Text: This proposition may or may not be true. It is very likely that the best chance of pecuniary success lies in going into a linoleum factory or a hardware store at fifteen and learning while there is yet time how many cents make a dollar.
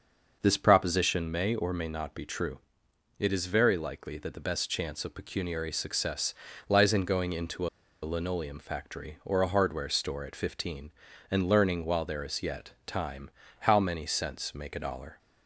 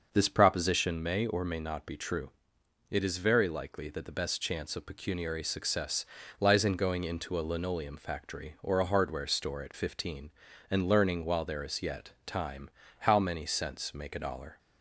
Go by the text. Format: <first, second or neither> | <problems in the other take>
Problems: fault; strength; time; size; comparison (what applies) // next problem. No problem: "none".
second | starts louder than the rest; until 1.4 s; 6 dB; also in the second // pauses between "success" and "lies"; slight; at 6.3 s; 0.36 s long; slight in the second // pauses between "into" and "a"; slight; at 7.6 s; 0.35 s long // pauses between "time" and "how"; slight; at 13.2 s; 0.32 s long; slight in the second